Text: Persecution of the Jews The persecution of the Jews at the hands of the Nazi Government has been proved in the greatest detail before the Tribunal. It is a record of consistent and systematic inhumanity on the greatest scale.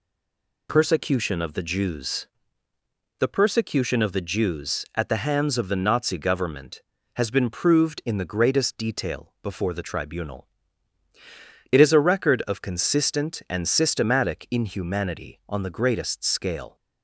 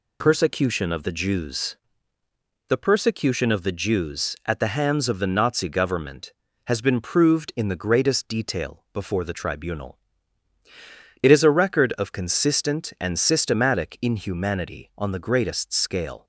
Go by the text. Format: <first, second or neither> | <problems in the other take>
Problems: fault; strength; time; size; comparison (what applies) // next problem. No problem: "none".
second | stays silent before the first word; slight; until 0.6 s; 0.6 s long // pauses between "Jews" and "The"; noticeable; at 2.2 s; 0.90 s long; noticeable in the second